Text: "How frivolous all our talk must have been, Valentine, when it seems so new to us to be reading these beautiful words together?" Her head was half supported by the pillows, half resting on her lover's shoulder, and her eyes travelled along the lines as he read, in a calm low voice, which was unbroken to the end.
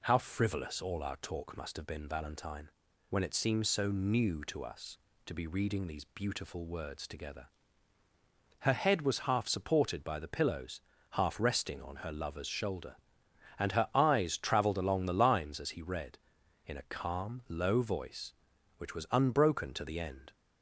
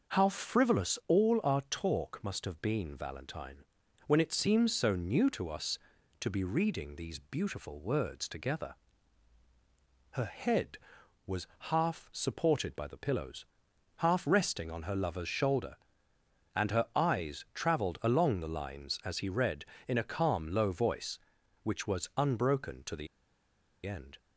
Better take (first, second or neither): first